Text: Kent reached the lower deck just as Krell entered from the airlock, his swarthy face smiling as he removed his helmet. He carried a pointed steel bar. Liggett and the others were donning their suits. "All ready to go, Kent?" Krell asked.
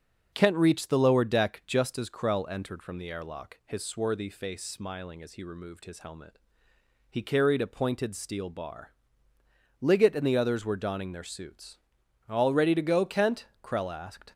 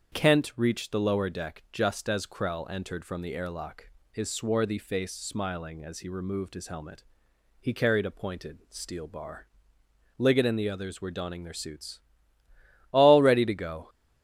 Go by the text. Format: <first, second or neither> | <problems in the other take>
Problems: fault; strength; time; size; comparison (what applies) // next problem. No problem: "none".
first | starts louder than the rest; strong; until 1.1 s; 7.5 dB; also in the first // stops before "Kent Krell asked"; at 13.8 s